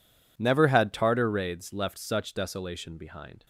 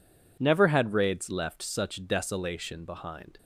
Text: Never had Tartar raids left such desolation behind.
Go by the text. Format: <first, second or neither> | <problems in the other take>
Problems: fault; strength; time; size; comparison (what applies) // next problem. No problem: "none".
first | skips "Tartar"; at 0.9 s